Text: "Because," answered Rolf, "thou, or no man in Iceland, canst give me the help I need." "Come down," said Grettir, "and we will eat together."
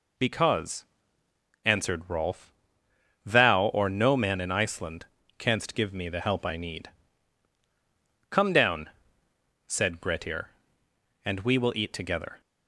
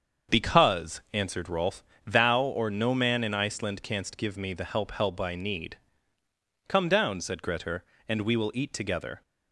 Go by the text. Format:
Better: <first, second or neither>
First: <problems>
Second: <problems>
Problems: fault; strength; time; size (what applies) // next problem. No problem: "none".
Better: first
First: none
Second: starts louder than the rest; until 1.4 s; 7 dB // says "help" twice; at 4.9 s